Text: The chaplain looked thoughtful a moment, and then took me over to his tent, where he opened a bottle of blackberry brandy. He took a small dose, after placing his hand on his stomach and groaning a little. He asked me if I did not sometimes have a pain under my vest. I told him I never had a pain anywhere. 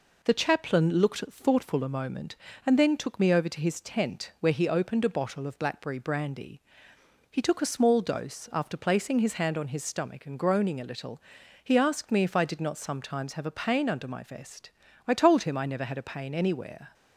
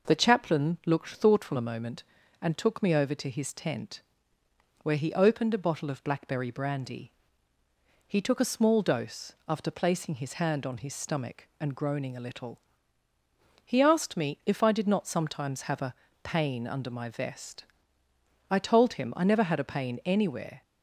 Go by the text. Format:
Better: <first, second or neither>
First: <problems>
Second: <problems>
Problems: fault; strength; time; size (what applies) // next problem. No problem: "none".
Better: first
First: none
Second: skips "then"; at 2.5 s // pauses between "a" and "pain"; slight; at 15.9 s; 0.28 s long